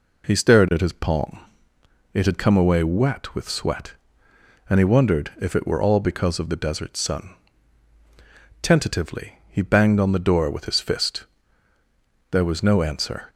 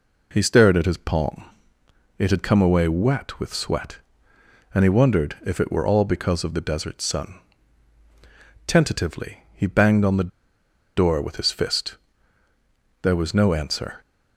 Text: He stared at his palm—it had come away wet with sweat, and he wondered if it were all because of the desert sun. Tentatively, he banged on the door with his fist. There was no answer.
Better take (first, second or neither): first